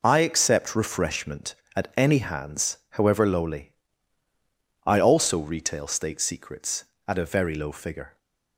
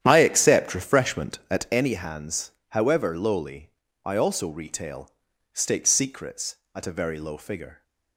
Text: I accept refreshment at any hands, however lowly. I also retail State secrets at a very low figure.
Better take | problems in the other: first | starts louder than the rest; strong; until 1.7 s; 10 dB // pauses between "retail" and "State"; at 5.1 s; 0.42 s long

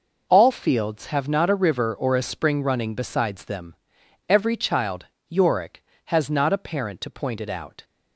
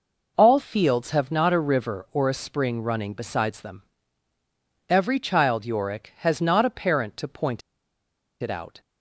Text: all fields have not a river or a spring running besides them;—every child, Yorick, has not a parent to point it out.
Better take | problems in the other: first | pauses between "point" and "it"; noticeable; at 7.6 s; 0.81 s long

